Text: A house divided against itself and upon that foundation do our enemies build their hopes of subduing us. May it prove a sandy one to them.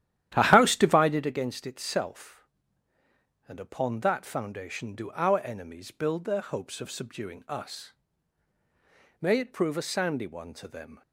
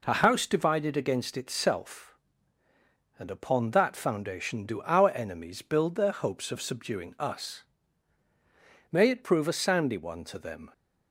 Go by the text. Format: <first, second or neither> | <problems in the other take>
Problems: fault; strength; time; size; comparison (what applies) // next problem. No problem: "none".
second | starts louder than the rest; strong; until 1.3 s; 12 dB